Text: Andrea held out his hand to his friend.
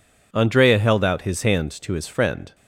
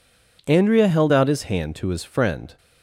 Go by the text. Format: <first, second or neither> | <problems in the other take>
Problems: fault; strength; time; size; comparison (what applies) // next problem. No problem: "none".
neither | none